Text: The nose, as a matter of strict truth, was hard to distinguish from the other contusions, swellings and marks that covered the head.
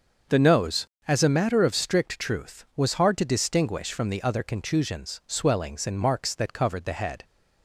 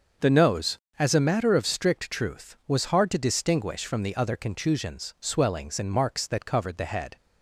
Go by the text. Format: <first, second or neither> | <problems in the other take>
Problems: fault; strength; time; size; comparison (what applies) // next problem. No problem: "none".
neither | starts louder than the rest; the same in both